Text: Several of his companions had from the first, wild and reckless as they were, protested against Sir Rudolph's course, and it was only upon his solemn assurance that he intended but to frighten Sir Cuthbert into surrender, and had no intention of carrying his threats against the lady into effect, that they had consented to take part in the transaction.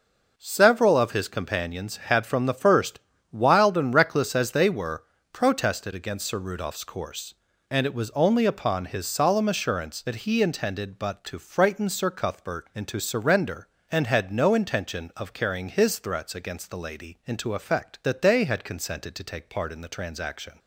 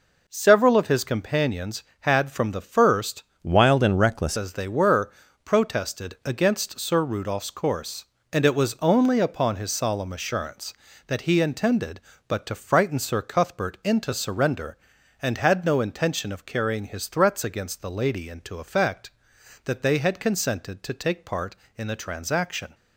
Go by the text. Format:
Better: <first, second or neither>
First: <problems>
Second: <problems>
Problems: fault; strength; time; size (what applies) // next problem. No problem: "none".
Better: first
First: none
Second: changes voice from "wild" to "reckless"; from 3.4 to 4.3 s; 0.9 s long